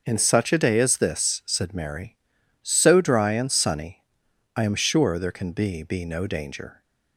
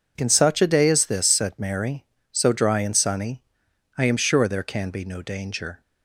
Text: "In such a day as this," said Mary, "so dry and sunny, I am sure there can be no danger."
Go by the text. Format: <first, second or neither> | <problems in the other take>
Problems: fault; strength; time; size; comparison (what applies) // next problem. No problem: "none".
second | says "be" twice; at 5.8 s